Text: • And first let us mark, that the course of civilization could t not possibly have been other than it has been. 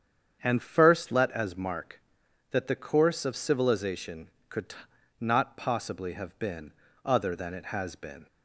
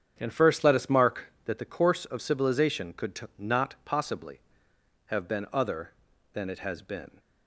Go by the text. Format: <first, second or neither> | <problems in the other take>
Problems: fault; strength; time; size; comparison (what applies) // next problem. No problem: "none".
second | starts louder than the rest; strong; until 1.4 s; 8 dB; strong in the second // says "as" for "us"; at 1.3 s // pauses between "t" and "not"; at 4.7 s; 0.44 s long // pauses between "been" and "other"; slight; at 6.7 s; 0.32 s long